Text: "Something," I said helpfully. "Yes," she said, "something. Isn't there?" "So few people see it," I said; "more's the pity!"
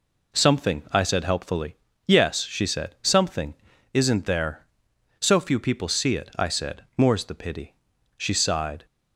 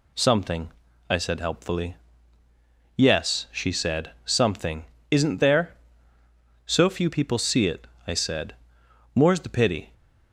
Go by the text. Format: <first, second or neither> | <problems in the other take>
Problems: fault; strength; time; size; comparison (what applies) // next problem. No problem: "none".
second | goes on to say "She sighed"; noticeable; from 8.1 s on; 0.70 s long